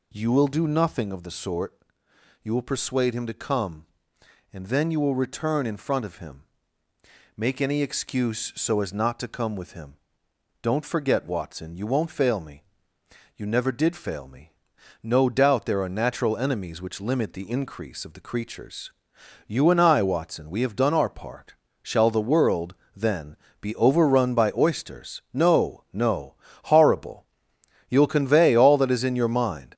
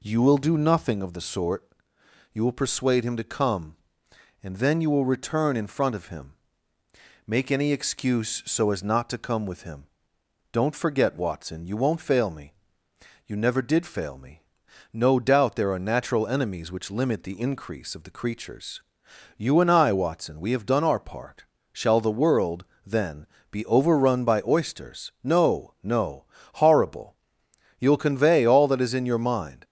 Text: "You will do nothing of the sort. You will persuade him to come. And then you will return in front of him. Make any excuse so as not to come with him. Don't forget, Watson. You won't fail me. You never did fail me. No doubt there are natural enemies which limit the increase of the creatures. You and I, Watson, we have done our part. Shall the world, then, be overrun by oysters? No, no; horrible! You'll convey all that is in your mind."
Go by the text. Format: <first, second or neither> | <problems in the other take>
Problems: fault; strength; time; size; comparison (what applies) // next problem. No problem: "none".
second | gets louder; noticeable; throughout; 5 dB